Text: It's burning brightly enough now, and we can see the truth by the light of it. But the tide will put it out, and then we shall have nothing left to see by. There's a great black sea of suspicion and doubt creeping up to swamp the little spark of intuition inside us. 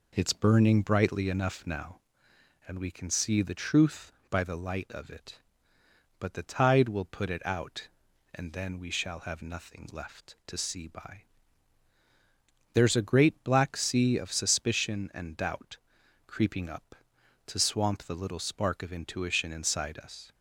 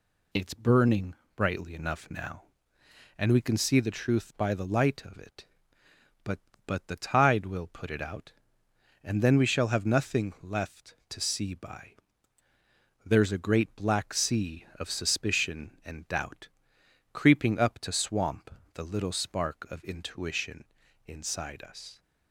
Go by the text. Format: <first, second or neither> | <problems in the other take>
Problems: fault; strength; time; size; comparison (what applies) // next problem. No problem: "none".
first | pauses between "burning" and "brightly"; slight; at 1.1 s; 0.22 s long // says "But" twice; at 6.6 s // pauses between "doubt" and "creeping"; noticeable; at 16.4 s; 0.64 s long; noticeable in the first // pauses between "swamp" and "the"; slight; at 18.4 s; 0.22 s long // pauses between "intuition" and "inside"; at 20.6 s; 0.42 s long